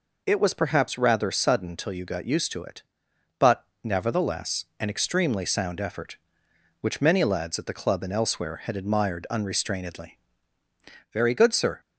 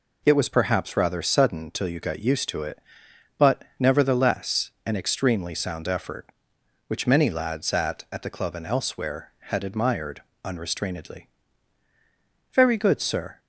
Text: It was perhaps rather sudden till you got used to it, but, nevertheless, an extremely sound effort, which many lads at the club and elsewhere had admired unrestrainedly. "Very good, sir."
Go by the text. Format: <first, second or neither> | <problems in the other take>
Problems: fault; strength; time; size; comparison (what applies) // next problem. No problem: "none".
first | says "at" twice; at 8.1 s // pauses between "admired" and "unrestrainedly"; slight; at 10.2 s; 0.24 s long